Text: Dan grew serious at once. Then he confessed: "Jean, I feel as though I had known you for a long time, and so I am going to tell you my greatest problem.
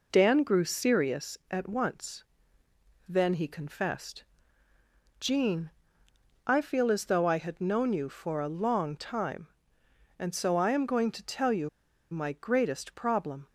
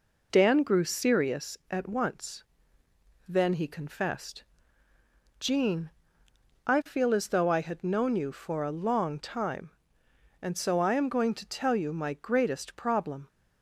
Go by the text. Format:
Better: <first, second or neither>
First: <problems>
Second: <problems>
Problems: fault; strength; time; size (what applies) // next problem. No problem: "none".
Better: second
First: pauses between "you" and "my"; at 11.6 s; 0.42 s long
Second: none